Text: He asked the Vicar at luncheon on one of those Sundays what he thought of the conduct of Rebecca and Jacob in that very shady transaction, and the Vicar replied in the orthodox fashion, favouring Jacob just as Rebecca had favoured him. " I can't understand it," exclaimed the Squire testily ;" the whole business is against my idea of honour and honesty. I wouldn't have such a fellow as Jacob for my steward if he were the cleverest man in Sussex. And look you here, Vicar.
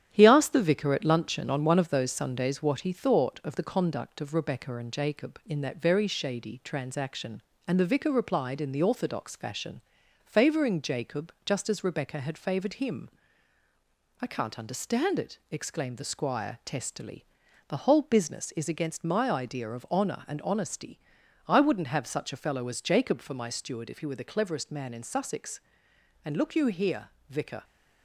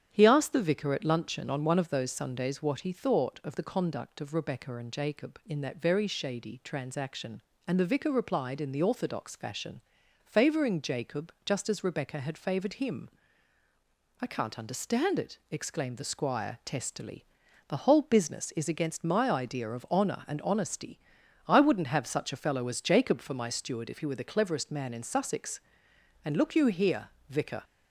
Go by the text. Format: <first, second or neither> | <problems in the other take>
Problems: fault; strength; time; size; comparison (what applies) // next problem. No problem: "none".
second | gets quieter; noticeable; throughout; 4 dB // starts louder than the rest; strong; until 1.1 s; 10 dB; strong in the second